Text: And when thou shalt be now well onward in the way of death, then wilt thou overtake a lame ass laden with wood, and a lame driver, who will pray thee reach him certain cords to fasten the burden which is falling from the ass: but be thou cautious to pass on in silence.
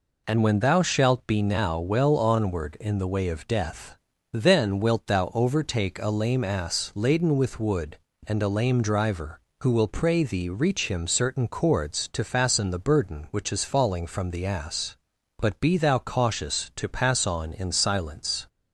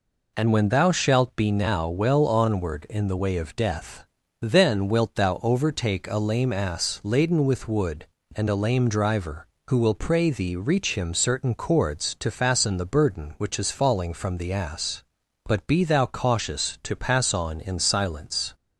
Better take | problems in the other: neither | none

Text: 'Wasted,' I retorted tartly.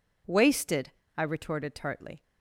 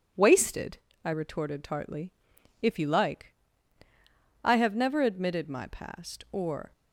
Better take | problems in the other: first | goes on to say "If you like I have never admitted my past or"; strong; from 2.6 s on; 4.1 s long

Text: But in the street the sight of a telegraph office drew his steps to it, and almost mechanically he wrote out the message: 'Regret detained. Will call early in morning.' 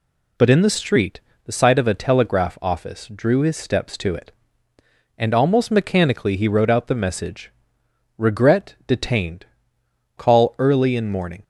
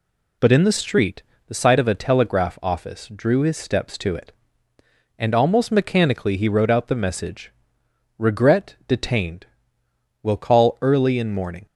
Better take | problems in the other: second | pauses between "street" and "the"; slight; at 1.2 s; 0.24 s long; slight in the second // skips "Will"; at 9.8 s

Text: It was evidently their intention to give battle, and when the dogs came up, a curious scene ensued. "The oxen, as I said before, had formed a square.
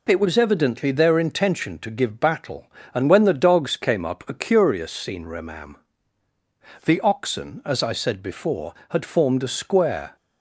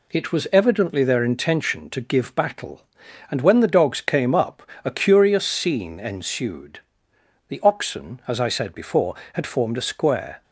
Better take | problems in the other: second | says "remam" for "ensued"; at 5.2 s

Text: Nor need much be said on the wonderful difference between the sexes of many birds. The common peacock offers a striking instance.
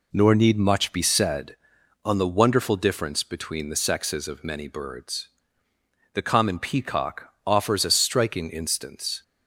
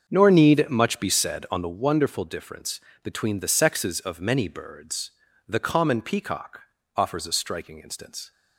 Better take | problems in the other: first | starts louder than the rest; until 1.8 s; 6.5 dB // pauses between "difference" and "between"; slight; at 2.7 s; 0.24 s long // pauses between "peacock" and "offers"; slight; at 6.6 s; 0.34 s long; slight in the first

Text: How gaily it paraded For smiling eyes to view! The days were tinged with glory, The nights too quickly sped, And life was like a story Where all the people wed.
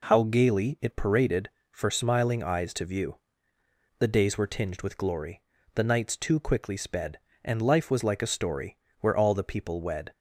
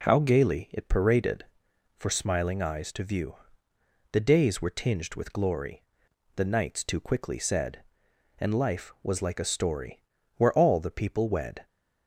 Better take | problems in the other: first | says "said" for "sped"; at 7.3 s // pauses between "story" and "Where"; slight; at 10.0 s; 0.36 s long; slight in the first

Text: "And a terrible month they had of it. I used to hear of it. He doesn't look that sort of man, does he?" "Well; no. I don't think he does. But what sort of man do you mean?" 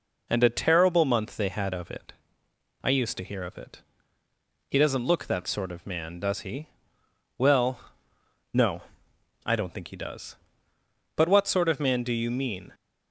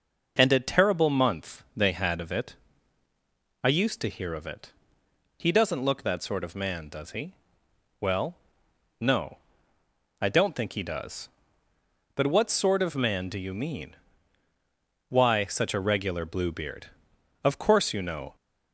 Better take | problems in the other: first | goes on to say "Why such a regular Bluebeard Of course you know"; strong; from 15.0 s on; 3.2 s long

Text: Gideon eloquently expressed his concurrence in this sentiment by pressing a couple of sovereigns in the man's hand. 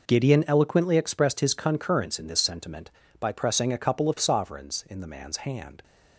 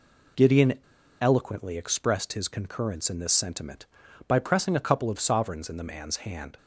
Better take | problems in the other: first | pauses between "Gideon" and "eloquently"; at 0.7 s; 0.41 s long

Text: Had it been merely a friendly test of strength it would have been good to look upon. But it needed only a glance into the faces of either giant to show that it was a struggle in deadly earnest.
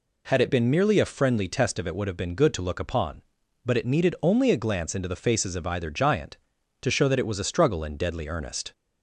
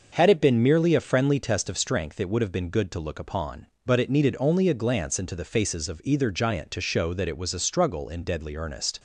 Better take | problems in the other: second | skips "strength"; at 1.8 s

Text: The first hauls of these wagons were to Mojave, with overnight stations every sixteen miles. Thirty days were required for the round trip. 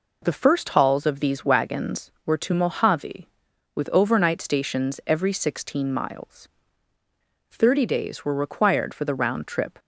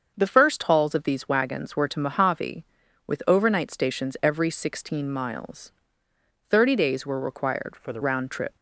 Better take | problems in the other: first | starts louder than the rest; until 1.1 s; 7 dB // changes voice from "for" to "the"; from 7.7 to 7.9 s; 0.2 s long

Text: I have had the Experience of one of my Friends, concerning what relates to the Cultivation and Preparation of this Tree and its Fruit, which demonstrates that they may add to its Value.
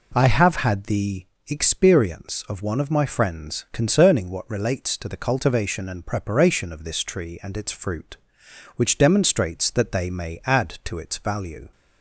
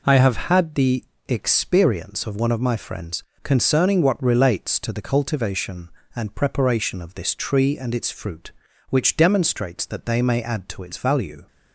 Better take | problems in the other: neither | pauses between "the" and "Experience"; slight; the same in both

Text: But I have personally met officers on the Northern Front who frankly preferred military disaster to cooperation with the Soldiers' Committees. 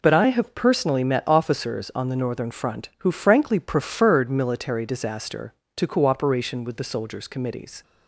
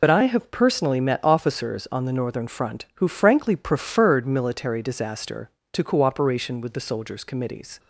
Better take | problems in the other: first | loses the start of "But"; at 0.0 s; 40 ms

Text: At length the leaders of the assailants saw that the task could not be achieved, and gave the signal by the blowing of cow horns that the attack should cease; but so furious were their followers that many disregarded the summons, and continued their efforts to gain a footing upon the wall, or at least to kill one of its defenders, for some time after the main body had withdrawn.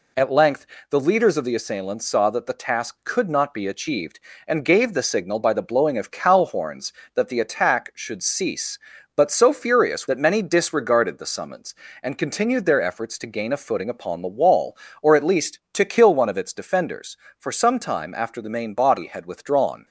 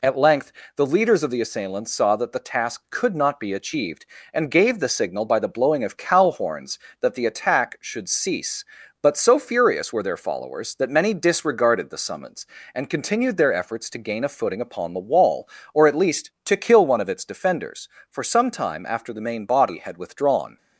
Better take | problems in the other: second | pauses between "length" and "the"; slight; at 0.6 s; 0.24 s long; slight in the second // skips "were their followers"; at 10.0 s

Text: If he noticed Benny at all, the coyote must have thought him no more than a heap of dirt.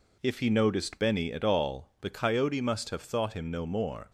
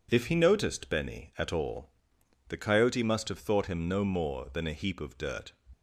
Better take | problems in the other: second | stops before "than a heap of dirt"; at 4.0 s

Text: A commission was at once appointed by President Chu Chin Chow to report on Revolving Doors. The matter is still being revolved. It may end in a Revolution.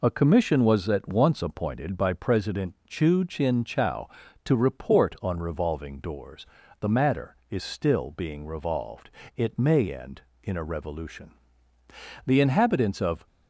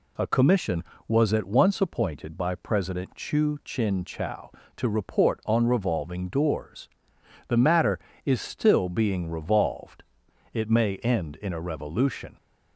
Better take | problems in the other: second | goes on to say "The inhabitants of"; noticeable; from 12.2 s on; 1.0 s long

